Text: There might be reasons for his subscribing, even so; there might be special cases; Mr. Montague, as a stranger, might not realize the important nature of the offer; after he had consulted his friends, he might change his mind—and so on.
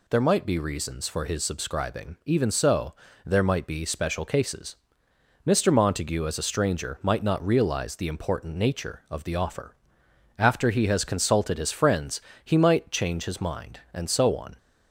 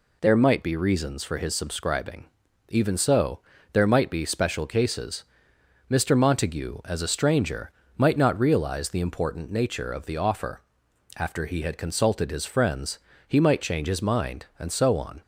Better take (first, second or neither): second